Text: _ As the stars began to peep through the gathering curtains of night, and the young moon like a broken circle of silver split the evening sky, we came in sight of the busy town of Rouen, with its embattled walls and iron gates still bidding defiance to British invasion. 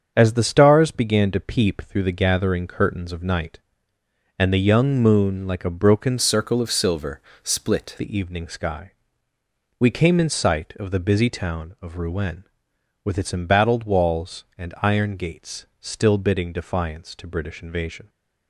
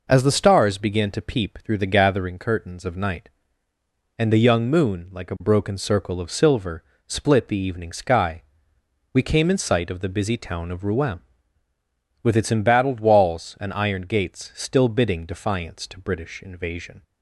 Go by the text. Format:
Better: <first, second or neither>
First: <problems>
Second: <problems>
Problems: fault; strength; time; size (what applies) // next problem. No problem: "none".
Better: second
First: starts louder than the rest; strong; until 1.1 s; 7 dB // changes voice from "circle" to "split"; from 6.1 to 7.9 s; 1.8 s long // pauses between "silver" and "split"; slight; at 7.1 s; 0.24 s long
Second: pauses between "silver" and "split"; slight; at 6.8 s; 0.24 s long